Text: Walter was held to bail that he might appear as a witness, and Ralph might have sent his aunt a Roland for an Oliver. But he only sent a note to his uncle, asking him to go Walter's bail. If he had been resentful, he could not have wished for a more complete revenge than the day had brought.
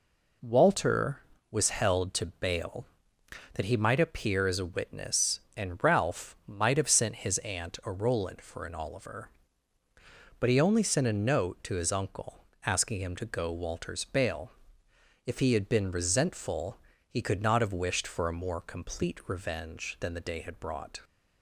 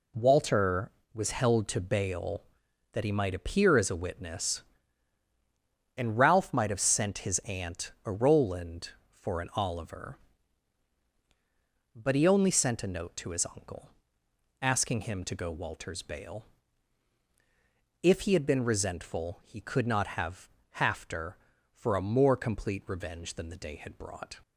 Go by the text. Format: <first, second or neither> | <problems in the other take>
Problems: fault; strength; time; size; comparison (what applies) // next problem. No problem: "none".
first | says "hafter" for "wished"; at 20.7 s